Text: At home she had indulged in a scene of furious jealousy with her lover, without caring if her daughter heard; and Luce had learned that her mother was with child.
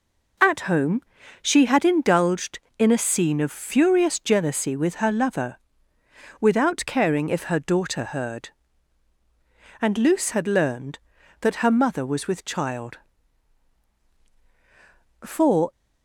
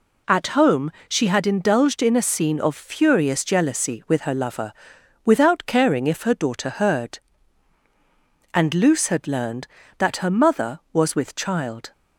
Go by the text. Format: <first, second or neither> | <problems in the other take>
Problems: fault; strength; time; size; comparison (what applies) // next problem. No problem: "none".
second | pauses between "home" and "she"; at 1.0 s; 0.40 s long; slight in the second // goes on to say "For"; slight; from 15.2 s on; 0.48 s long